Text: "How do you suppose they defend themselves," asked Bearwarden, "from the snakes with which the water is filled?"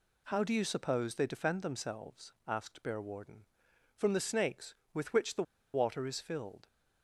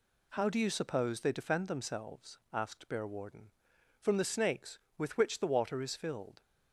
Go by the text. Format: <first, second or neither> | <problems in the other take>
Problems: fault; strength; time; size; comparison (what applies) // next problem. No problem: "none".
second | pauses between "the" and "water"; slight; at 5.4 s; 0.31 s long